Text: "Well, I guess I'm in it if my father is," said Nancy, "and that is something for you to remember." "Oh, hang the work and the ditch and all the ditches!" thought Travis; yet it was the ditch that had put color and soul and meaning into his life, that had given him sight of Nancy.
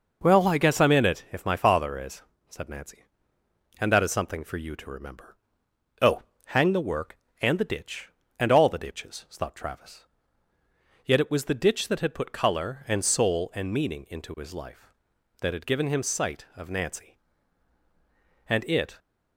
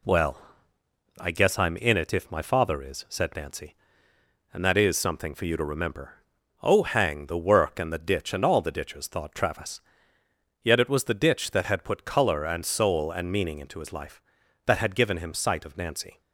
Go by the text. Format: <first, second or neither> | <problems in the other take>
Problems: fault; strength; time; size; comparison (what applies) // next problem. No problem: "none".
second | goes on to say "And it"; from 18.4 s on; 0.50 s long